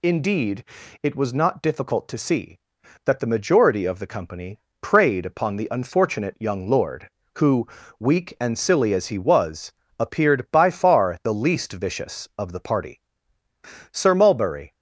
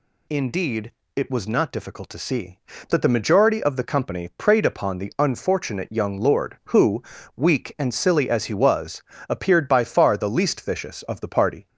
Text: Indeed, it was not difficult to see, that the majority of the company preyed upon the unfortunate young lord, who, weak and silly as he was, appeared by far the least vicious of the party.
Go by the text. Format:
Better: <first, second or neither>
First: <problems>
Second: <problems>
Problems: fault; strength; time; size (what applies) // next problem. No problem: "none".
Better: second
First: pauses between "company" and "preyed"; slight; at 4.5 s; 0.20 s long // goes on to say "Sir Mulberry"; noticeable; from 13.8 s on; 0.82 s long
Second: none